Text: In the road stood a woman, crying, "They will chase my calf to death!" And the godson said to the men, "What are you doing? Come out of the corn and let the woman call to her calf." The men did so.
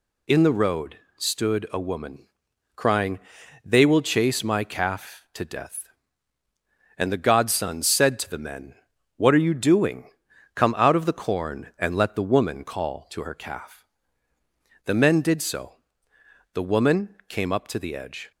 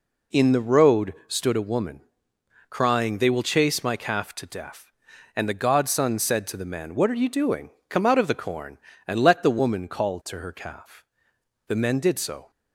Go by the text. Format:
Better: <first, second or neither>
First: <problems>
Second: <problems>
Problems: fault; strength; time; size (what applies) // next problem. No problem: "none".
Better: second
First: pauses between "road" and "stood"; slight; at 0.9 s; 0.20 s long // goes on to say "The woman came up to the edge"; strong; from 16.5 s on; 1.7 s long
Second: none